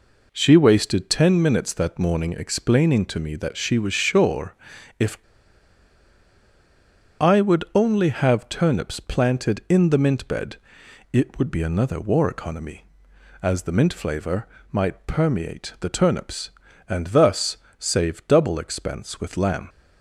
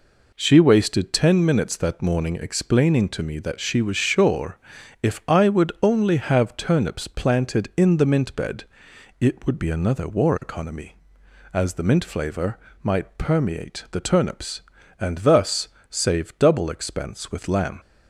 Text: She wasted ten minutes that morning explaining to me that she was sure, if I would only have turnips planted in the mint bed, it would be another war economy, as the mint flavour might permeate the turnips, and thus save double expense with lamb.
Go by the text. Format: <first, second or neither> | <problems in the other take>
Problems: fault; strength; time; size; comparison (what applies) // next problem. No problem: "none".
second | pauses between "if" and "I"; strong; at 5.1 s; 2.0 s long // pauses between "flavour" and "might"; slight; at 14.4 s; 0.26 s long; slight in the second // pauses between "thus" and "save"; slight; at 17.5 s; 0.22 s long; slight in the second